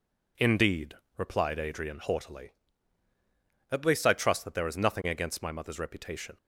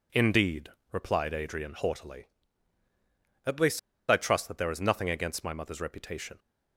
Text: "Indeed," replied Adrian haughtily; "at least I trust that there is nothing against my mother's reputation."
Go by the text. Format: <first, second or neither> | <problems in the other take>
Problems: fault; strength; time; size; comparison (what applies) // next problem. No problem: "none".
first | pauses between "least" and "I"; slight; at 3.7 s; 0.28 s long